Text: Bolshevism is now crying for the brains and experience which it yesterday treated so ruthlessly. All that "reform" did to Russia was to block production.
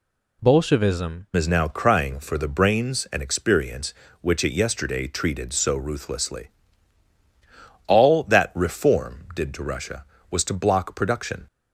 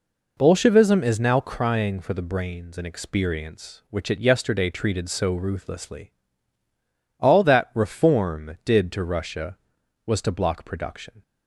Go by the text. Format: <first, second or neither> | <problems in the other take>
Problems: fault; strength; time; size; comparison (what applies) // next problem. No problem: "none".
second | changes voice at "is"; from 1.3 s on; 10.1 s long